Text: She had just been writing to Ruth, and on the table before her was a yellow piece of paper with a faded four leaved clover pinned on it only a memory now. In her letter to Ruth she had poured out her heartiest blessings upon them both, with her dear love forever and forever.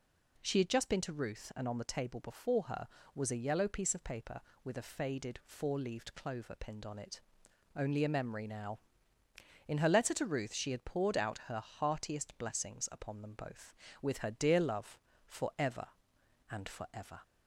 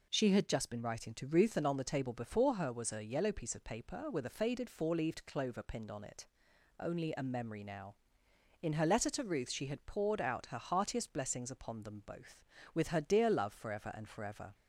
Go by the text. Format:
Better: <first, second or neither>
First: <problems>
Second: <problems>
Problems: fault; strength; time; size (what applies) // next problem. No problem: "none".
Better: second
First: skips "writing"; at 1.0 s // pauses between "it" and "only"; noticeable; at 7.2 s; 0.58 s long // pauses between "love" and "forever"; slight; at 14.9 s; 0.28 s long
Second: pauses between "it" and "only"; noticeable; at 6.2 s; 0.54 s long